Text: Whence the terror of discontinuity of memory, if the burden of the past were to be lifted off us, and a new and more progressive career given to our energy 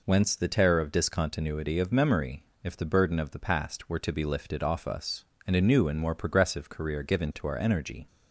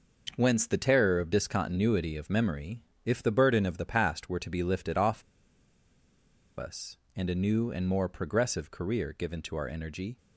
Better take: first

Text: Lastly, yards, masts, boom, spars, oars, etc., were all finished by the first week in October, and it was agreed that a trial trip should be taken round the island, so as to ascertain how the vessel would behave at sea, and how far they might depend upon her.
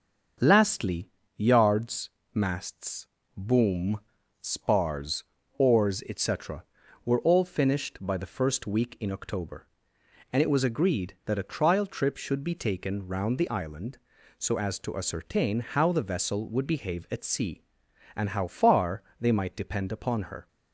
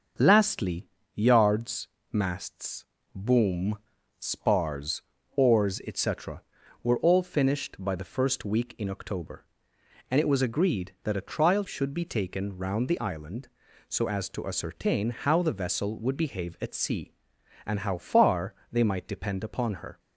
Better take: first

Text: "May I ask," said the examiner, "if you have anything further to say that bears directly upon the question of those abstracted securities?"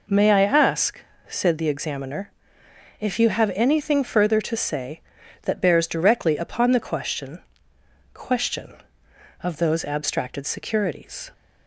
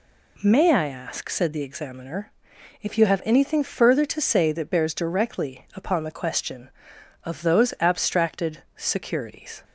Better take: second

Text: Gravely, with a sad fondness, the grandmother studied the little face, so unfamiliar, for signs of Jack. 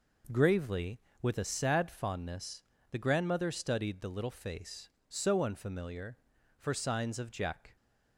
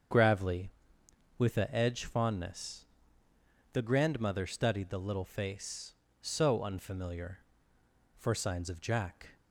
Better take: first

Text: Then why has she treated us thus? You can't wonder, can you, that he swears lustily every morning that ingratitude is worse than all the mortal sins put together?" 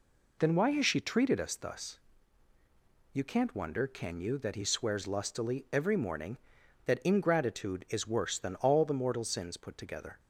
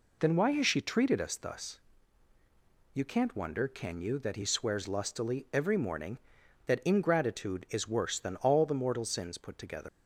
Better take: first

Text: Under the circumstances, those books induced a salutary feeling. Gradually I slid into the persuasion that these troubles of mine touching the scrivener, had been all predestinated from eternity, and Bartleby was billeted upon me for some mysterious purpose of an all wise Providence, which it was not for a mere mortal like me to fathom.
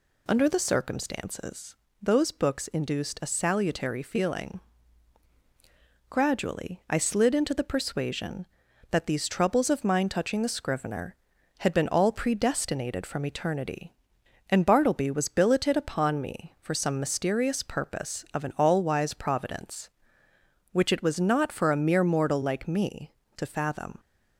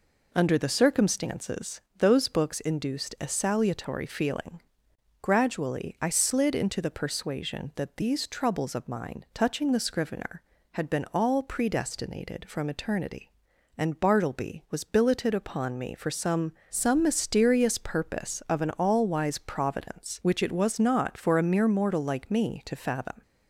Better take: first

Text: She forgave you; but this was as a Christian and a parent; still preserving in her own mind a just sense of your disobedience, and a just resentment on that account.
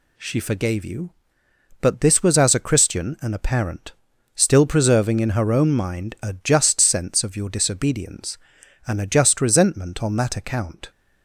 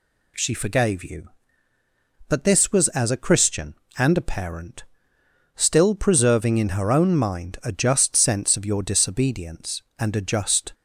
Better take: first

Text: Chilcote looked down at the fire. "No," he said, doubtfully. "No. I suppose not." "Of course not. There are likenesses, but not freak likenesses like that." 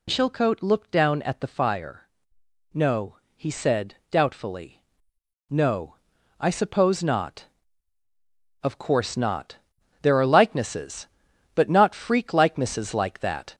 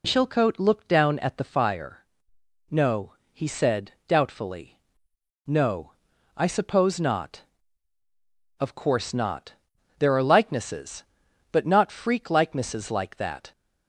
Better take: second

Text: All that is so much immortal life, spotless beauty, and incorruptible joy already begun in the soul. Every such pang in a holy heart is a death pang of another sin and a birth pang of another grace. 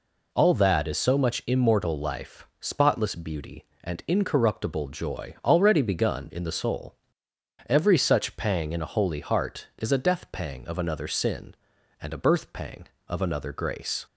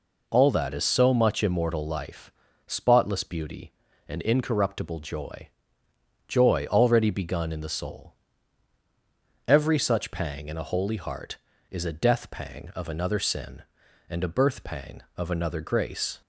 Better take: first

